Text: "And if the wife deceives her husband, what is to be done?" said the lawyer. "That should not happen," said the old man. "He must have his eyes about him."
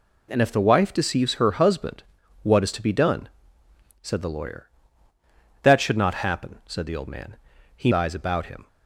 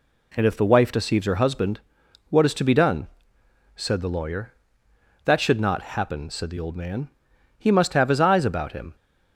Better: second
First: skips "must have his"; at 7.9 s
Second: none

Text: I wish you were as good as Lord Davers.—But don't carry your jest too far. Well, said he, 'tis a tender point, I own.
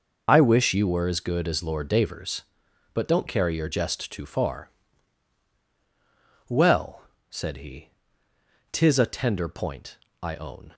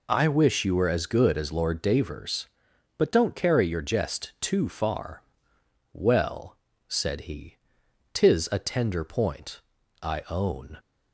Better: second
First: loses the start of "I"; at 0.2 s; 25 ms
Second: none

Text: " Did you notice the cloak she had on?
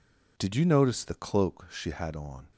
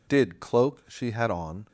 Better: first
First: none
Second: skips "you notice the"; at 0.4 s

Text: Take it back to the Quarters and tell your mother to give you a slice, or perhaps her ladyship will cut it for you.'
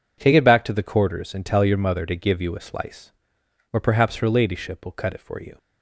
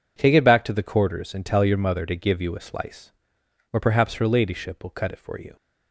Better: neither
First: none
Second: none

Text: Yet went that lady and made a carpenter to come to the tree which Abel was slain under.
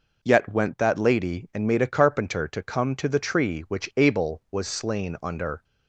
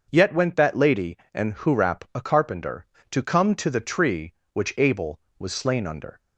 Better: first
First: none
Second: starts louder than the rest; until 1.1 s; 6 dB // says "hurap" for "made"; at 1.5 s

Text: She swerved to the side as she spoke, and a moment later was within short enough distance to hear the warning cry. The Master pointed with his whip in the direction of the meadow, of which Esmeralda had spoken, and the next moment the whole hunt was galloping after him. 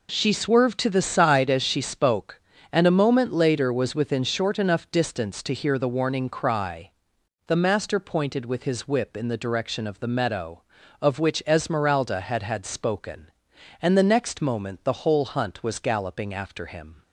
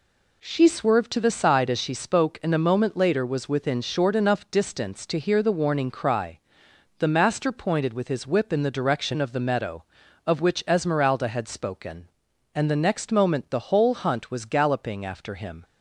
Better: second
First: says "had" twice; at 12.4 s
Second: none

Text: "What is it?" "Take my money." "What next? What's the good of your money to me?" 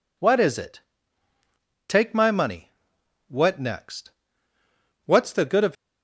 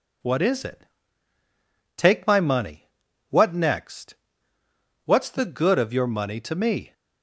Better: second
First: stops before "your money to me"; at 5.7 s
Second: none

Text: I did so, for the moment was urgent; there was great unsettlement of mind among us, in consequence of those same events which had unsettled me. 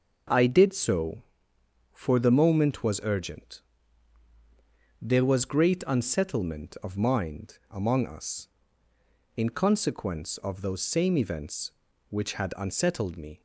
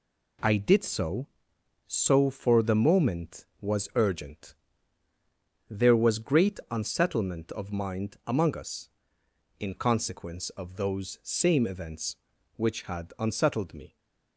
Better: first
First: none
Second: says "so" twice; at 1.9 s

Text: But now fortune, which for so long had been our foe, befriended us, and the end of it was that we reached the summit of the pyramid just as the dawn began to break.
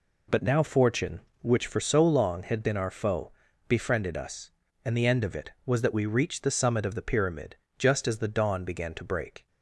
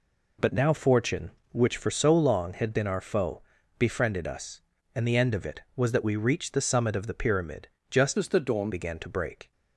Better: first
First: pauses between "pyramid" and "just"; slight; at 7.5 s; 0.22 s long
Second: pauses between "pyramid" and "just"; slight; at 7.6 s; 0.22 s long // changes voice from "as" to "dawn"; from 8.1 to 8.7 s; 0.6 s long

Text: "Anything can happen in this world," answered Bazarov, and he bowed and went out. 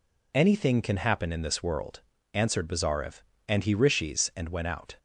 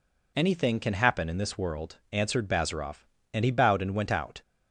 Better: second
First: says "rishis" for "bowed"; at 3.7 s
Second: none

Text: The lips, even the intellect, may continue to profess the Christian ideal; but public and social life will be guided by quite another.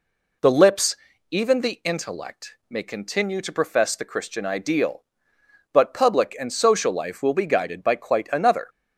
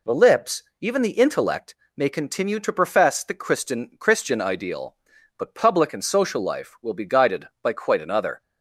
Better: first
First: none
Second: says "Christian" twice; at 3.9 s

